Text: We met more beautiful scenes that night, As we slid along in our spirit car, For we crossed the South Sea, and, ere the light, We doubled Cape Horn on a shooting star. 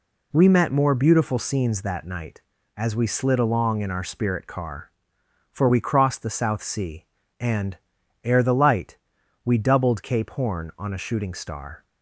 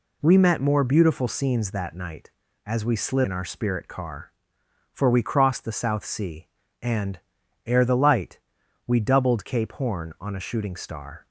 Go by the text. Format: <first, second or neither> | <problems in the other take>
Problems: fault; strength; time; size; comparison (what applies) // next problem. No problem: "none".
first | skips "along"; at 3.2 s